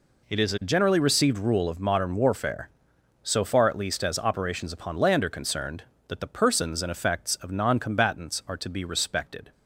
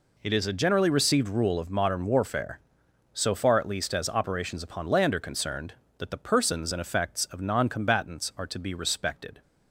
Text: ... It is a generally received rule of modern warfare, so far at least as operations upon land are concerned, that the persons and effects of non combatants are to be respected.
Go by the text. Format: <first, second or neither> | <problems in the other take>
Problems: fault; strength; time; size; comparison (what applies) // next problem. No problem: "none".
neither | none